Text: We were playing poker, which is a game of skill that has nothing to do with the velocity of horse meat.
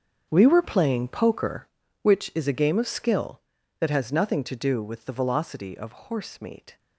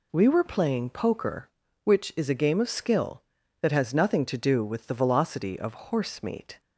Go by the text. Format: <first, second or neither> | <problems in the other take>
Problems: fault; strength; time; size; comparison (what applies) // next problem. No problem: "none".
second | gets quieter; strong; throughout; 14.5 dB